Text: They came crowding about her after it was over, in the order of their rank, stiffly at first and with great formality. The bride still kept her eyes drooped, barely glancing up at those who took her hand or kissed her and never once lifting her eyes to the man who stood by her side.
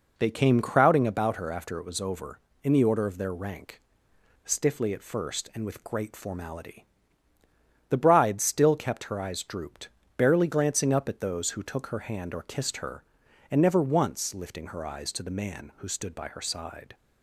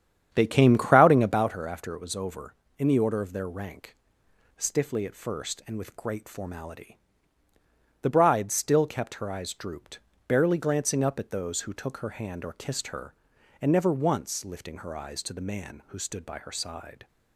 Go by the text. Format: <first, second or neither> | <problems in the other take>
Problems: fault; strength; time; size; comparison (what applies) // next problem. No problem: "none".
first | starts louder than the rest; strong; until 1.6 s; 9 dB